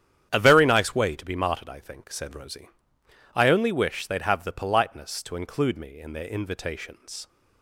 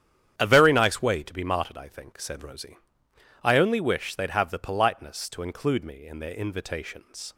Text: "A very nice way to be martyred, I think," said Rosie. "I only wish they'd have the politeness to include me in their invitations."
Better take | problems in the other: neither | starts louder than the rest; strong; the same in both

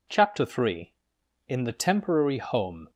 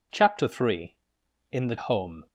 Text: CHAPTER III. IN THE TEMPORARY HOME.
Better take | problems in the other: first | skips "TEMPORARY"; at 1.7 s

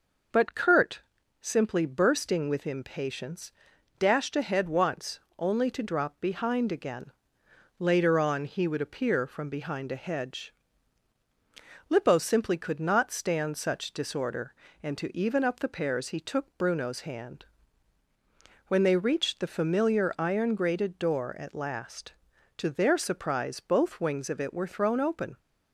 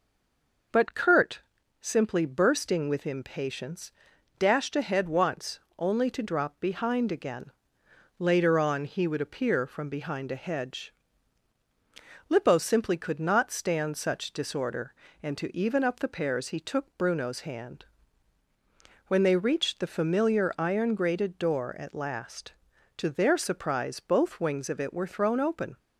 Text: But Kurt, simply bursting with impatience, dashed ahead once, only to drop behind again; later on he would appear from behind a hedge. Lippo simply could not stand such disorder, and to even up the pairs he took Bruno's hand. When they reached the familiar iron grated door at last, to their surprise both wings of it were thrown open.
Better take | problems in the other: first | stays silent before the first word; slight; until 0.7 s; 0.7 s long

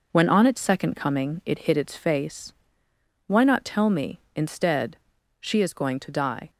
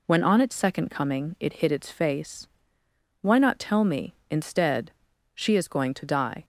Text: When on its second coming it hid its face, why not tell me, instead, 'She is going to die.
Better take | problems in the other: second | gets quieter; noticeable; throughout; 5.5 dB

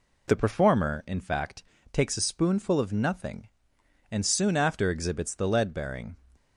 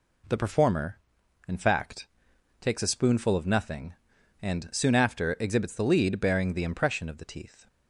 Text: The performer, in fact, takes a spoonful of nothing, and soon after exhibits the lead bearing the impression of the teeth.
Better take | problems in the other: second | stops before "the impression of the teeth"; at 6.3 s

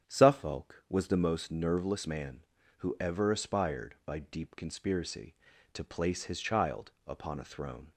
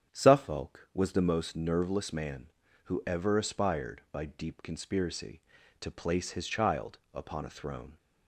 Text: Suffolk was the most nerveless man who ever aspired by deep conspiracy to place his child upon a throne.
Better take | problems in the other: neither | starts louder than the rest; strong; the same in both // pauses between "child" and "upon"; slight; the same in both

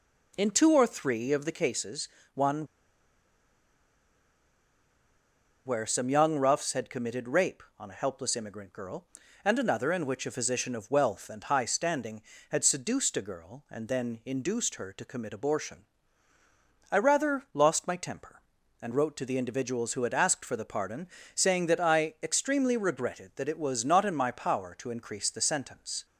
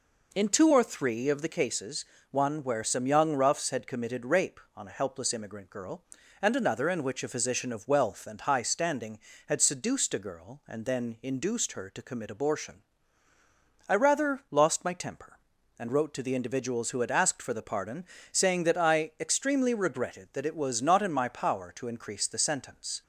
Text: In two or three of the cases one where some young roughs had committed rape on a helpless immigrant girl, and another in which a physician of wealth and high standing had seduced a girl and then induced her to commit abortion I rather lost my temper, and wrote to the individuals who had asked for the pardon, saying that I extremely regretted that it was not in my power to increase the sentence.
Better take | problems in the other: second | pauses between "cases" and "one"; slight; at 2.0 s; 0.26 s long; slight in the second // pauses between "one" and "where"; strong; at 2.6 s; 2.9 s long // pauses between "abortion" and "I"; at 15.8 s; 1.0 s long; also in the second

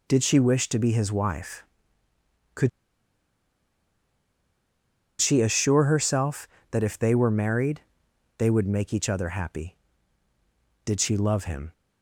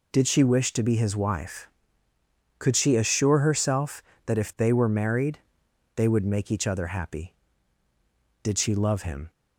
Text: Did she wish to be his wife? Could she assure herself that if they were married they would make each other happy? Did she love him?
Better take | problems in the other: second | pauses between "Could" and "she"; strong; at 2.6 s; 2.5 s long // pauses between "married" and "they"; noticeable; at 7.8 s; 0.56 s long; noticeable in the second

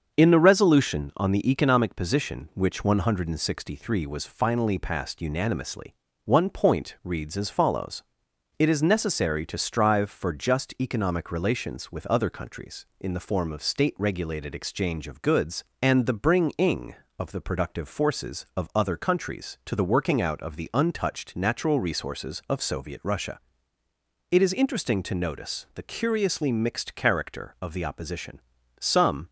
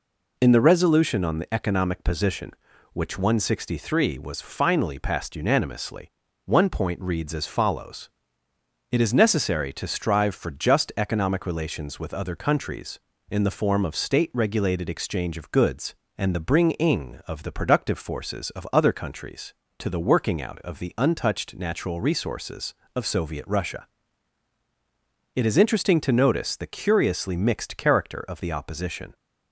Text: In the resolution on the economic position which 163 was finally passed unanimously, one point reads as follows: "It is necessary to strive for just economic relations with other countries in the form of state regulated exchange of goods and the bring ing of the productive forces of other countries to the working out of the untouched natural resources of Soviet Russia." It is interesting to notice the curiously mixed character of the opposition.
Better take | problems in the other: second | starts louder than the rest; until 1.2 s; 6.5 dB // goes on to say "Some"; from 28.7 s on; 0.50 s long

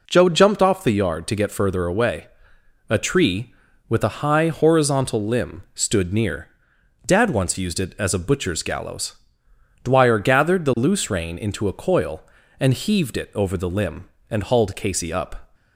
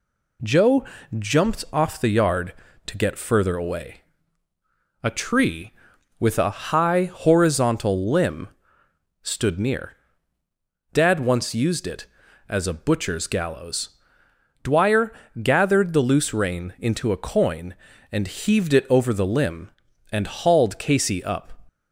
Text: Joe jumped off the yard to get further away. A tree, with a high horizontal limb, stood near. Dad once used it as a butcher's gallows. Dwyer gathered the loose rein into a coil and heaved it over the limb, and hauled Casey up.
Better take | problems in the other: first | pauses between "Joe" and "jumped"; slight; at 0.8 s; 0.32 s long // pauses between "Dwyer" and "gathered"; slight; at 15.1 s; 0.30 s long // says "coin" for "coil"; at 17.1 s

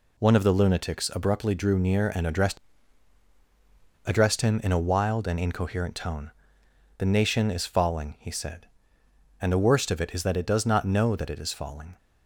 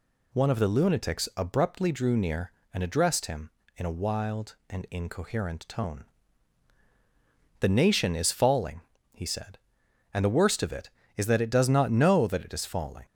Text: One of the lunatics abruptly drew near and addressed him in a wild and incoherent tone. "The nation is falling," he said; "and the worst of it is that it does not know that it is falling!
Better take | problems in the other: second | says "addressed" twice; at 4.0 s

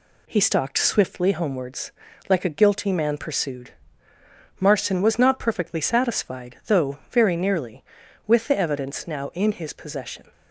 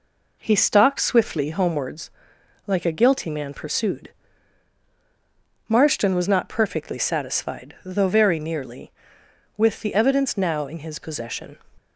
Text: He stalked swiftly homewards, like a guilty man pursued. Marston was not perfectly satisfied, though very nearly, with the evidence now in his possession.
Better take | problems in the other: neither | none

